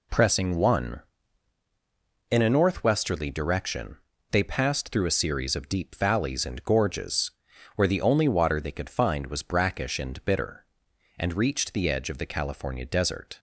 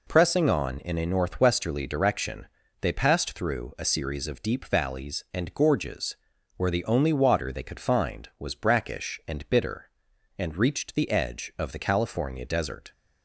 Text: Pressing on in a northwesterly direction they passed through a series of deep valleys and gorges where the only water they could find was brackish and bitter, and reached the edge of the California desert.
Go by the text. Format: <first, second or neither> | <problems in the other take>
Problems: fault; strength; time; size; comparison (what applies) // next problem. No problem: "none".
second | says "one" for "on"; at 0.5 s // pauses between "direction" and "they"; slight; at 3.9 s; 0.34 s long; slight in the second // pauses between "gorges" and "where"; noticeable; at 7.3 s; 0.46 s long; also in the second